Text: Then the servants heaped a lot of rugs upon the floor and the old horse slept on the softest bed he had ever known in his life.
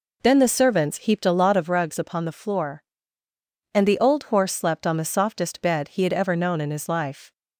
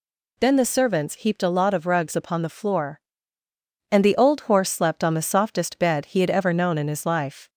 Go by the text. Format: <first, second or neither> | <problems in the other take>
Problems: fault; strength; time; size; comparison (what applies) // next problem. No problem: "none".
second | starts louder than the rest; noticeable; until 1.8 s; 4 dB